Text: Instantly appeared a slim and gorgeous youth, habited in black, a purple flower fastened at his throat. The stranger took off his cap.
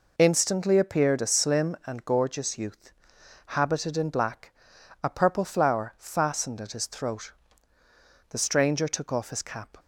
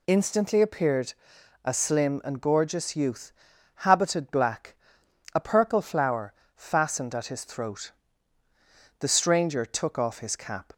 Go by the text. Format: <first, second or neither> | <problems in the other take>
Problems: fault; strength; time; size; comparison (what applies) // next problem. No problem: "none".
first | pauses between "appeared" and "a"; noticeable; at 1.1 s; 0.50 s long // skips "in"; at 4.3 s // pauses between "flower" and "fastened"; slight; at 6.3 s; 0.24 s long